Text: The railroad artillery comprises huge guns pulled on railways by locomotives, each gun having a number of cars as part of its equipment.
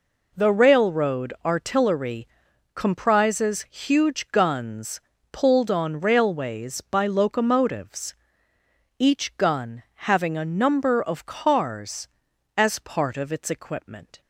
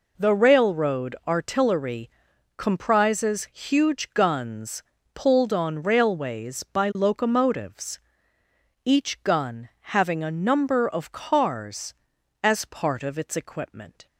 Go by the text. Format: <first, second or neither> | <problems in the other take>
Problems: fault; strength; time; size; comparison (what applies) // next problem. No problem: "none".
neither | pauses between "artillery" and "comprises"; noticeable; the same in both // pauses between "guns" and "pulled"; slight; the same in both